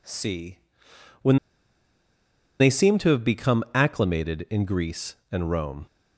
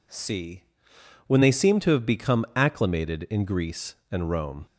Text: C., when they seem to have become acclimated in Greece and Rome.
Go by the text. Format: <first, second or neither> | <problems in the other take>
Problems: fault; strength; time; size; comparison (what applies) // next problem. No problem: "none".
second | pauses between "when" and "they"; at 1.3 s; 1.2 s long